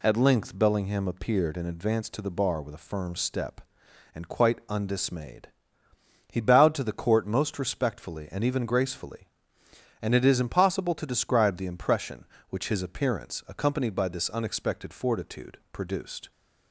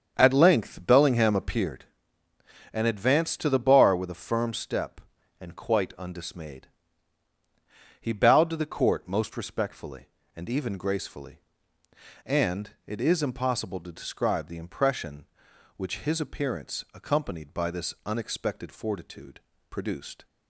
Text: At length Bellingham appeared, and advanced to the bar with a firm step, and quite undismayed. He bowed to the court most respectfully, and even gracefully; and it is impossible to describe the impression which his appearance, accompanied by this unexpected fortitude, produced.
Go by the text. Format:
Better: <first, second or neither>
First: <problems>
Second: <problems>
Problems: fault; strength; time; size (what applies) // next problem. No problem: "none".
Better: first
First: none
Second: starts louder than the rest; strong; until 1.9 s; 7.5 dB